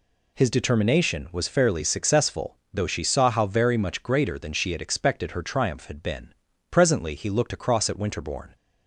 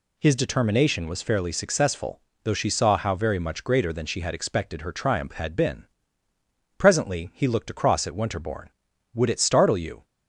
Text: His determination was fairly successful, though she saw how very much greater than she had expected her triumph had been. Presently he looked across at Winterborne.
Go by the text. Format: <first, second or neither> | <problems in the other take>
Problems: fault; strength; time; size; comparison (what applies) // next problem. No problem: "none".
first | goes on to say "Would it startle you"; noticeable; from 9.1 s on; 0.92 s long